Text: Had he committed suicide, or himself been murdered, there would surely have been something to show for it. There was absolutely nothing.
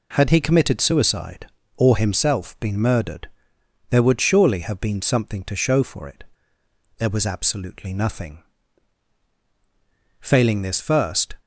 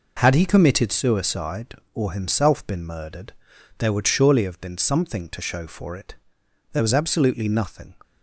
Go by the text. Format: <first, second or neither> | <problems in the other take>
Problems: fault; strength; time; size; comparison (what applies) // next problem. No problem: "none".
second | goes on to say "Failing this first"; noticeable; from 10.1 s on; 1.1 s long